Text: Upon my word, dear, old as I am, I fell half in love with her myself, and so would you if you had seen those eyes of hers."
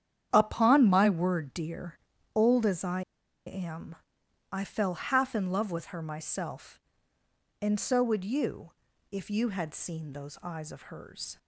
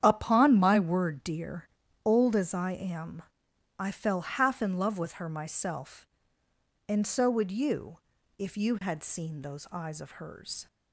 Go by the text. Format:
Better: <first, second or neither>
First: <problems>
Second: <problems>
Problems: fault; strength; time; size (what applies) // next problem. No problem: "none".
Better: second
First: starts louder than the rest; strong; until 1.3 s; 9.5 dB // pauses between "I" and "am"; at 3.0 s; 0.45 s long // pauses between "you" and "if"; at 8.7 s; 0.40 s long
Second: starts louder than the rest; strong; until 1.0 s; 9.5 dB // pauses between "you" and "if"; at 7.9 s; 0.40 s long